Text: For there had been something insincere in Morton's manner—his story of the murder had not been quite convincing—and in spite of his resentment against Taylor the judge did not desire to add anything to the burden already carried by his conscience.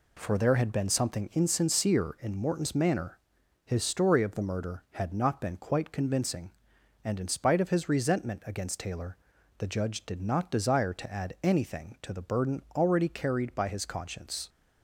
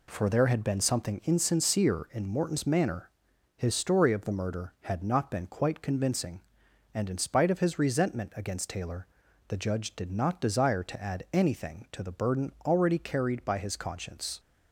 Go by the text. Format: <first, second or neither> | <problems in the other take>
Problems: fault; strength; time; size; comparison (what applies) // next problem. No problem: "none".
neither | pauses between "Taylor" and "the"; the same in both